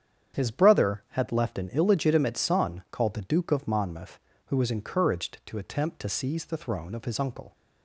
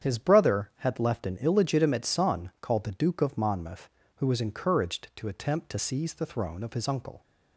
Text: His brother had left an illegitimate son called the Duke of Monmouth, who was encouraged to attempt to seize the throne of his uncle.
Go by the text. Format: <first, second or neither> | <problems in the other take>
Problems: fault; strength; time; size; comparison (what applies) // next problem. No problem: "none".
neither | starts louder than the rest; strong; the same in both